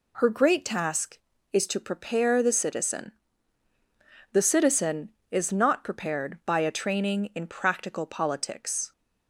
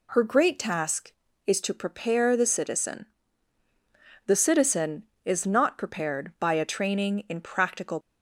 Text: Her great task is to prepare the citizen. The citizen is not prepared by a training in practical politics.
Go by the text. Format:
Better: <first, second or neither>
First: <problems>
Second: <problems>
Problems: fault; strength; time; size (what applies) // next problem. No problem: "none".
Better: first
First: none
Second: stops before "politics"; at 8.0 s